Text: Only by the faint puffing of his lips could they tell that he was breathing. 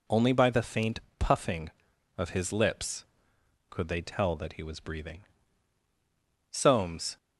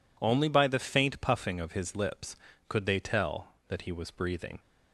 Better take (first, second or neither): second